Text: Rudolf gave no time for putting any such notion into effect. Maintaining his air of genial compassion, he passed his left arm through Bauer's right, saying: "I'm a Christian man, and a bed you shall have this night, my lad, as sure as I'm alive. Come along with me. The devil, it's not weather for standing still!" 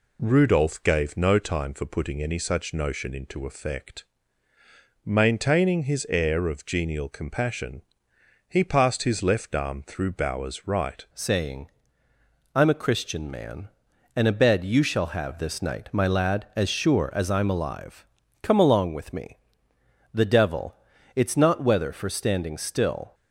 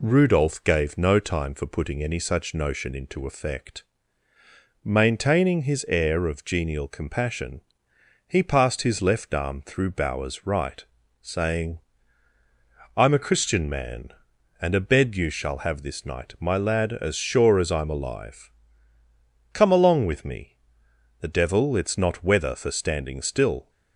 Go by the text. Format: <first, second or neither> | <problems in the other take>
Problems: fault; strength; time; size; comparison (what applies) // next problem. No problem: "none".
second | changes voice at "saying"; from 11.1 s on; 12.0 s long